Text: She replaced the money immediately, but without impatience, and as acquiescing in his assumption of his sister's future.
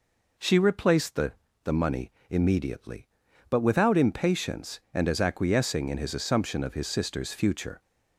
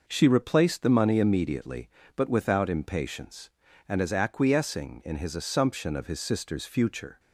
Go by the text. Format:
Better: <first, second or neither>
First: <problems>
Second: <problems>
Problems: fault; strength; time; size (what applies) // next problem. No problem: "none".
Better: second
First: says "the" twice; at 1.6 s // pauses between "money" and "immediately"; slight; at 2.1 s; 0.18 s long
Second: none